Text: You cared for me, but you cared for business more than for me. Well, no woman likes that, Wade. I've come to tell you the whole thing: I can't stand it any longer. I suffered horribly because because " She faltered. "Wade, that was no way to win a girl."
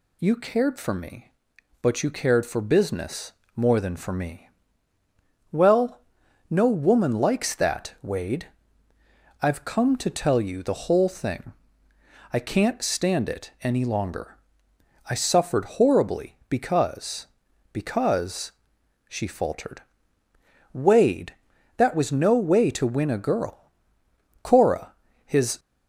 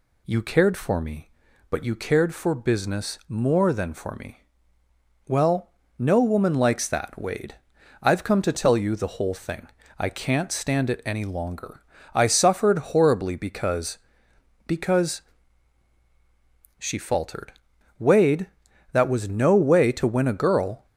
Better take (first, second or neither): second